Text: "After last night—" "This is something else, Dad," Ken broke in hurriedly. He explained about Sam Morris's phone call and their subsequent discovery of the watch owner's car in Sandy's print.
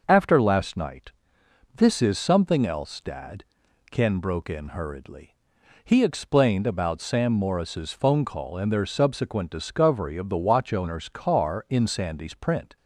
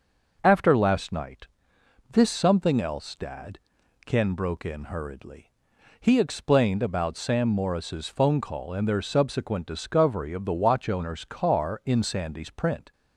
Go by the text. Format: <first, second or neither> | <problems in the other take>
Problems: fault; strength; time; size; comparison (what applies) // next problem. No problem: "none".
first | starts louder than the rest; noticeable; until 1.4 s; 6 dB; noticeable in the first // skips "is"; at 2.3 s